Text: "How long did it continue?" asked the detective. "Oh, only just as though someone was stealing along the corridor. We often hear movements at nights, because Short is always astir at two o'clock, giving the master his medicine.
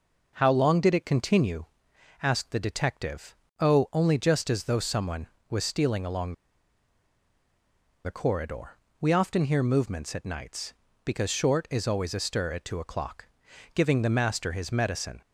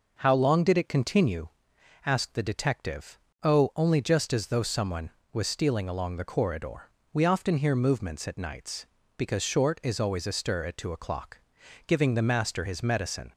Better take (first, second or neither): second